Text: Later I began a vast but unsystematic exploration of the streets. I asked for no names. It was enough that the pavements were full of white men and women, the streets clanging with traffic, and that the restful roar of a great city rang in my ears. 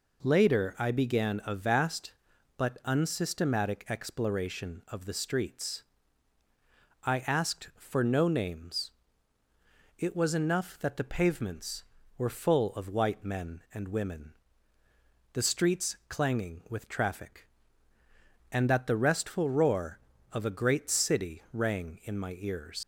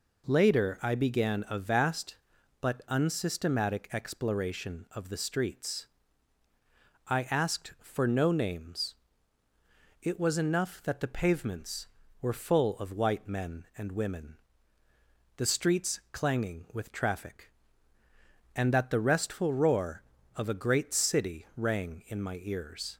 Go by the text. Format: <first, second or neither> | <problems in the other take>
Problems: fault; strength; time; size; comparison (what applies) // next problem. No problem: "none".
second | leaves "ears" unfinished; at 22.8 s; 100 ms